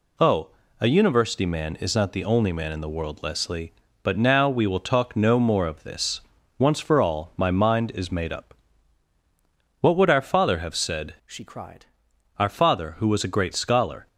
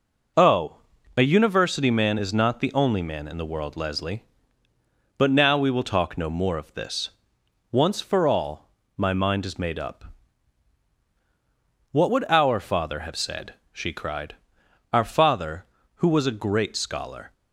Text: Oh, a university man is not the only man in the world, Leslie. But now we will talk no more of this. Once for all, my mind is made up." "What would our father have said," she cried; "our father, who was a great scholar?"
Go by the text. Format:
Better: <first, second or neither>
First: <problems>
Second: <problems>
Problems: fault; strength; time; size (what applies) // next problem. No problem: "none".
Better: second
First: changes voice from "she" to "cried"; from 11.2 to 11.8 s; 0.6 s long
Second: none